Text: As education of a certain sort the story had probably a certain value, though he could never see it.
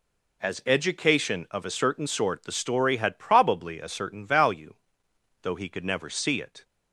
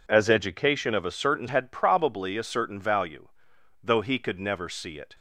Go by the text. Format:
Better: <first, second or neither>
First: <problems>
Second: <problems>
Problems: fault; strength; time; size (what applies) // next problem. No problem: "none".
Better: first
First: none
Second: skips "sort the story"; at 1.4 s